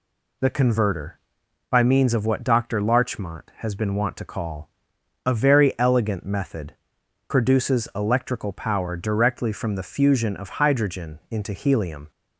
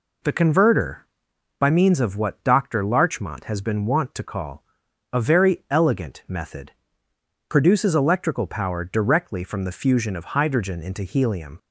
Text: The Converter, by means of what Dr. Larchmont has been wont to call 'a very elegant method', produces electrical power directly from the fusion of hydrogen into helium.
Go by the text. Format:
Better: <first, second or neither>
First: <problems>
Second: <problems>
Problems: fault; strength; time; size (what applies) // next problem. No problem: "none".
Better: neither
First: pauses between "call" and "a"; noticeable; at 4.6 s; 0.56 s long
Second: pauses between "call" and "a"; noticeable; at 4.6 s; 0.50 s long